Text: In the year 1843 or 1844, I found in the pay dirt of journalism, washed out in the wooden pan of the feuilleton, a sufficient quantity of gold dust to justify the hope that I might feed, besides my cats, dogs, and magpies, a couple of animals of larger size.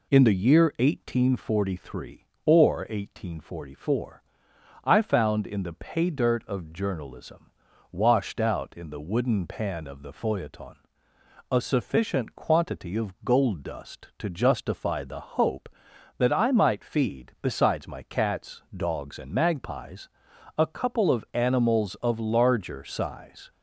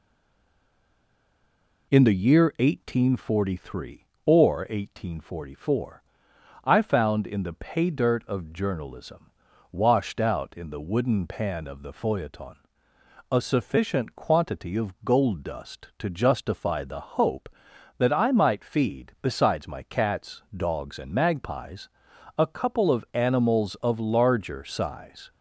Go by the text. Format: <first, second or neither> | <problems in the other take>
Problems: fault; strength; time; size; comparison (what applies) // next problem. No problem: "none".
first | stays silent before the first word; noticeable; until 1.9 s; 1.9 s long